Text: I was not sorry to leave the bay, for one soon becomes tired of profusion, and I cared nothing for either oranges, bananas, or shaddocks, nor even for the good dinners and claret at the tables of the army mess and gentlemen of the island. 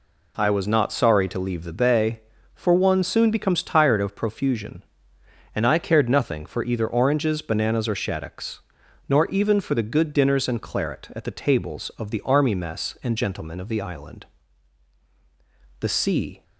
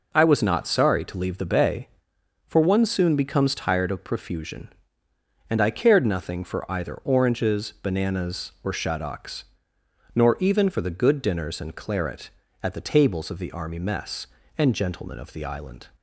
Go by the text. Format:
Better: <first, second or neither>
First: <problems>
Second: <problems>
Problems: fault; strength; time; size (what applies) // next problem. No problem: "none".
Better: second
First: goes on to say "The sea"; noticeable; from 15.8 s on; 0.62 s long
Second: none